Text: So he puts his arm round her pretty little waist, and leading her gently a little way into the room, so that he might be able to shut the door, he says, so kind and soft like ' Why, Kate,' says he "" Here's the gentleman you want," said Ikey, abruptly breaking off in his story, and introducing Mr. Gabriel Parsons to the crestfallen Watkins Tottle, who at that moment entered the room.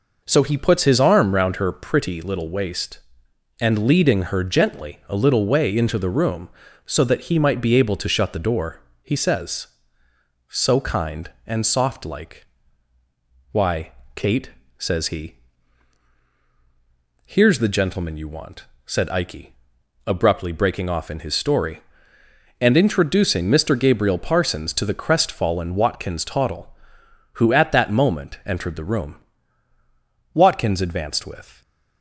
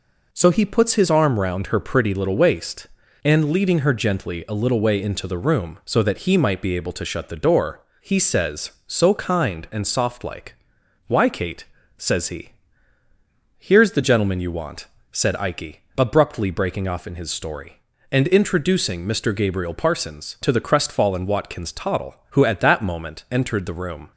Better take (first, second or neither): second